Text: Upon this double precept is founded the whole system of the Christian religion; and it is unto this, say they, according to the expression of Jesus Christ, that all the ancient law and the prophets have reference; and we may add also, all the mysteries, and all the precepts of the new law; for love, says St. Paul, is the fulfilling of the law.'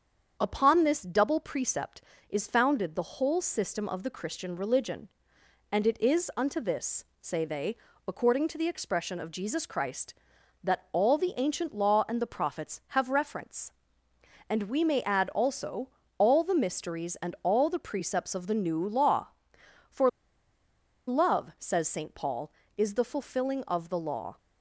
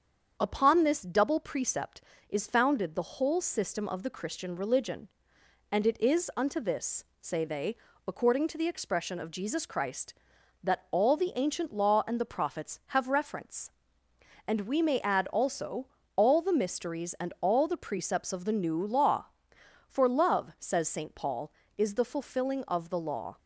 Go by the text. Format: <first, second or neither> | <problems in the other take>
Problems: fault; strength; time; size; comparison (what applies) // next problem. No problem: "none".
second | starts louder than the rest; strong; until 1.4 s; 7.5 dB; strong in the second // pauses between "for" and "love"; at 20.0 s; 0.99 s long